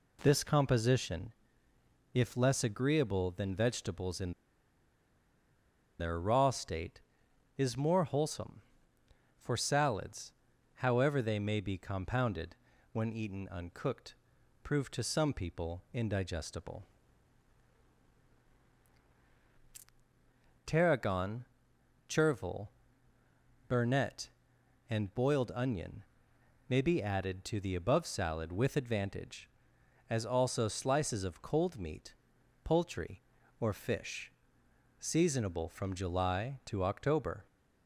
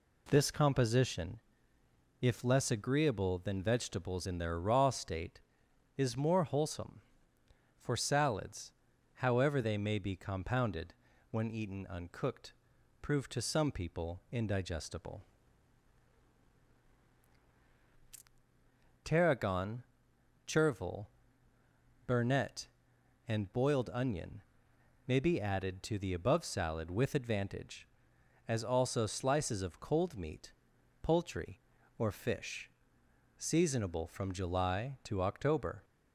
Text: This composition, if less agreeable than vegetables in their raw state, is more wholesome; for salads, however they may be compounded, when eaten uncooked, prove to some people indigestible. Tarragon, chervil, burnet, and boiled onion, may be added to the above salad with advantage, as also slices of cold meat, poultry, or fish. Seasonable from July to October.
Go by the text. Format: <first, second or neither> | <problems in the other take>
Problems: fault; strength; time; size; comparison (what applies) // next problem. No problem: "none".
second | pauses between "in" and "their"; strong; at 4.3 s; 1.6 s long